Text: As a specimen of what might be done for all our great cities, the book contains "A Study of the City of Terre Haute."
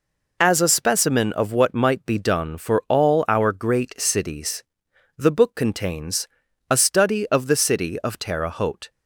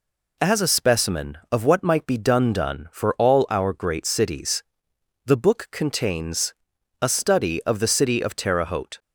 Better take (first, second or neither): first